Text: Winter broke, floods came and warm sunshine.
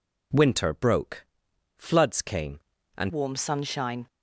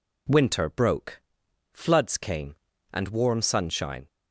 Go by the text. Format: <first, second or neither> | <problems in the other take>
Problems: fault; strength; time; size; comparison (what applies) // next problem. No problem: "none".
second | changes voice at "warm"; from 3.0 s on; 1.0 s long